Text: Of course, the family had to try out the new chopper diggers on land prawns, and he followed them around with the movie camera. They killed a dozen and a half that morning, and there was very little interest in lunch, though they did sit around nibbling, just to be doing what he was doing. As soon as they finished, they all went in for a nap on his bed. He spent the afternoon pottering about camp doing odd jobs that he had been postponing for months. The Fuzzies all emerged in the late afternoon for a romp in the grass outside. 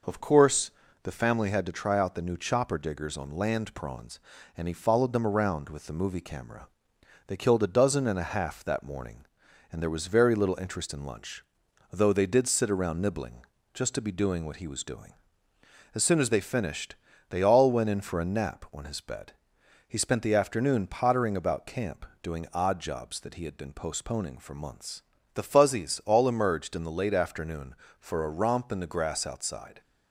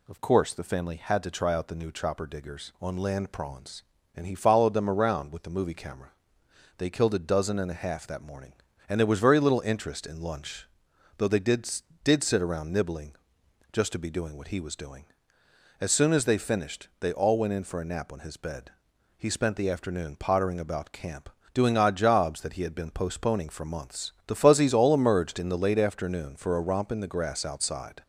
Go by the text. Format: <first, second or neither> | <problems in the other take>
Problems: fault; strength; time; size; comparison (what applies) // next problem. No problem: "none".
first | says "did" twice; at 12.0 s // pauses between "camp" and "doing"; slight; at 21.2 s; 0.24 s long; slight in the first